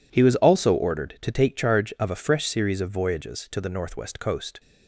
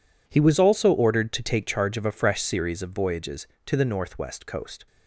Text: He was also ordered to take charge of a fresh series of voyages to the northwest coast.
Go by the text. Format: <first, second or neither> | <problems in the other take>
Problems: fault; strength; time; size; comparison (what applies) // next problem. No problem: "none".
neither | none